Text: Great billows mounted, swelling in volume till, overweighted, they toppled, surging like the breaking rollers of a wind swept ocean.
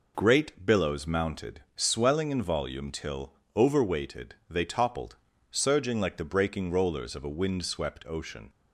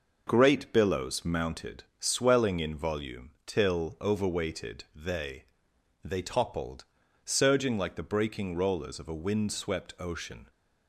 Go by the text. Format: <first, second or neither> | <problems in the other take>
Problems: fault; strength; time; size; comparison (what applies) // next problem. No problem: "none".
first | pauses between "volume" and "till"; slight; at 3.2 s; 0.16 s long // says "they" twice; at 6.0 s